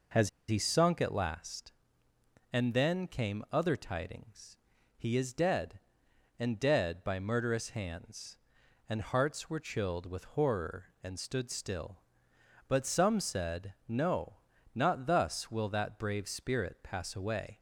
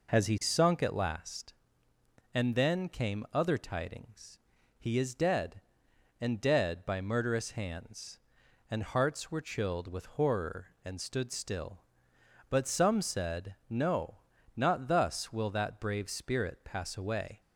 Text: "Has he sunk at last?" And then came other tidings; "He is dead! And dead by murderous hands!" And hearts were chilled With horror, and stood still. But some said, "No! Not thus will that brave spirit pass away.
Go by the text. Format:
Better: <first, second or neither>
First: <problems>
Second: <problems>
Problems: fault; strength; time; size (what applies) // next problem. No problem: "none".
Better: second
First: pauses between "Has" and "he"; slight; at 0.2 s; 0.20 s long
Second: none